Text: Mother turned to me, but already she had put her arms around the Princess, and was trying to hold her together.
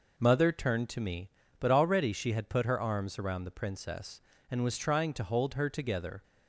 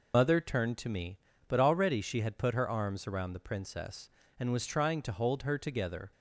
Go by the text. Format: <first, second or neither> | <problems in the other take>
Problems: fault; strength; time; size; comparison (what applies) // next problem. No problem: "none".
first | loses the start of "Mother"; at 0.1 s; 75 ms